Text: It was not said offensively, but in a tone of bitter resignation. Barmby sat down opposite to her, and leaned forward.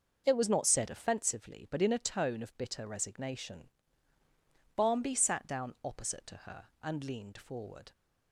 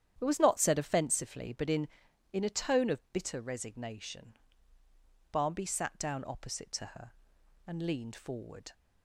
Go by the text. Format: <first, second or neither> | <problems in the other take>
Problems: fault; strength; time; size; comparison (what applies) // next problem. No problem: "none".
first | starts louder than the rest; strong; until 1.1 s; 10 dB // says "in" twice; at 2.3 s